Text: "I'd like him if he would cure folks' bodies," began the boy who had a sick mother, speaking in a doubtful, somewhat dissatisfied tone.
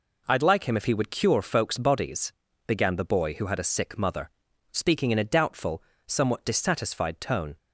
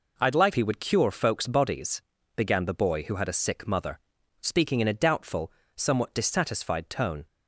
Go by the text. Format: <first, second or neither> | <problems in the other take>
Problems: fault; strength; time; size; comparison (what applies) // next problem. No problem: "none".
first | skips "him if"; at 0.5 s